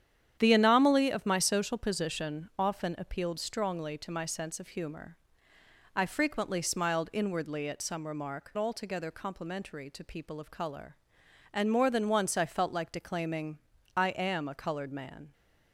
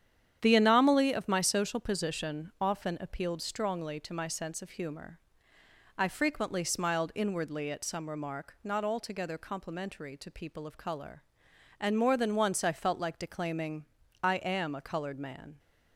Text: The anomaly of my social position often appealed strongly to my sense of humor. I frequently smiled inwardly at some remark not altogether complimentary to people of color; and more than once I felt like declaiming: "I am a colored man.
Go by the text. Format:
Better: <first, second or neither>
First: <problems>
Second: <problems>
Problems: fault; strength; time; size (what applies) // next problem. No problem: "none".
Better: second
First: starts louder than the rest; strong; until 1.4 s; 9.5 dB // skips "not"; at 8.5 s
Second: starts louder than the rest; strong; until 1.4 s; 9.5 dB